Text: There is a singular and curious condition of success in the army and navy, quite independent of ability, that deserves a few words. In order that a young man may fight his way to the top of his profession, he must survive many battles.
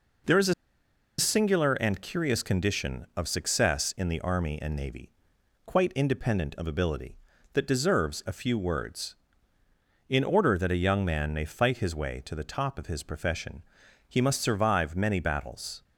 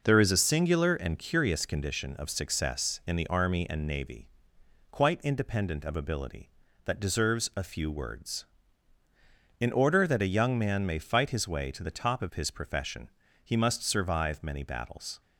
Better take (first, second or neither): second